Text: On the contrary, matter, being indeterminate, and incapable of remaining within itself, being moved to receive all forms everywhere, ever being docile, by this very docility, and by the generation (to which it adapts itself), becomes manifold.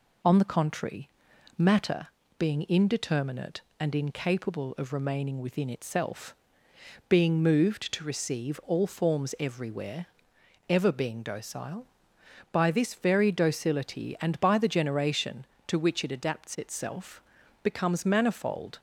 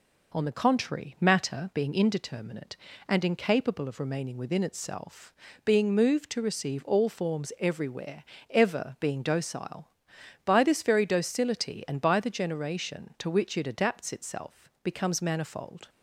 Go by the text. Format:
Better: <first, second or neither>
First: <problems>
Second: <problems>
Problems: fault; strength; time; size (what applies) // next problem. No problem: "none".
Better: neither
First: none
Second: none